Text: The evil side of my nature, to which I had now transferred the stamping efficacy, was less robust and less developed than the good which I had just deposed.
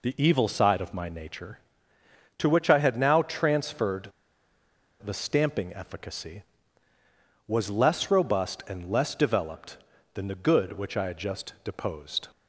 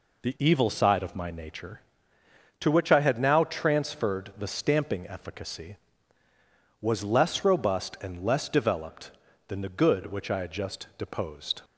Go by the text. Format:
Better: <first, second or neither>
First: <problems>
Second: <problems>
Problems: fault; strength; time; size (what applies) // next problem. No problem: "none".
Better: second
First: pauses between "transferred" and "the"; noticeable; at 4.0 s; 0.94 s long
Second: none